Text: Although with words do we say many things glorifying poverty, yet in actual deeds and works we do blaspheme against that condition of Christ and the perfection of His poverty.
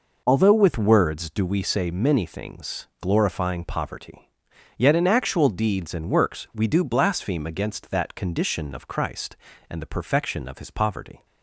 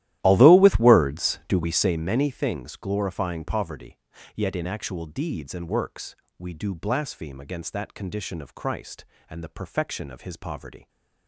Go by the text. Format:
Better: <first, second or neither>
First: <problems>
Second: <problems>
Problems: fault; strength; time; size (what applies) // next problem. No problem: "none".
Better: first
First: none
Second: starts louder than the rest; strong; until 2.1 s; 14 dB // pauses between "works" and "we"; slight; at 6.1 s; 0.24 s long